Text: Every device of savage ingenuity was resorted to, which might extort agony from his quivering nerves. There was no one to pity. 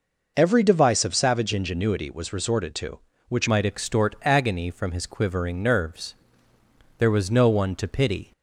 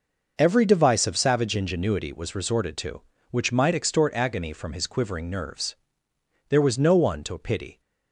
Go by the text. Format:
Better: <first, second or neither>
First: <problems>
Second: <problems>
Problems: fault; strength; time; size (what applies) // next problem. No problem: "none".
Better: second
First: changes voice at "might"; from 3.4 s on; 4.9 s long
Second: none